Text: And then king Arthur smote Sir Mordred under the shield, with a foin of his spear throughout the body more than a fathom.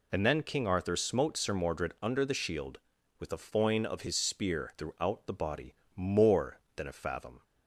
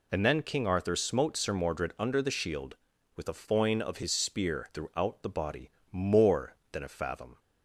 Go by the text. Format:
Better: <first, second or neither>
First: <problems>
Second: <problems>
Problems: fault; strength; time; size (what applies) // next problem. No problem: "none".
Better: neither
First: pauses between "body" and "more"; slight; at 5.7 s; 0.20 s long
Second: pauses between "body" and "more"; slight; at 5.7 s; 0.20 s long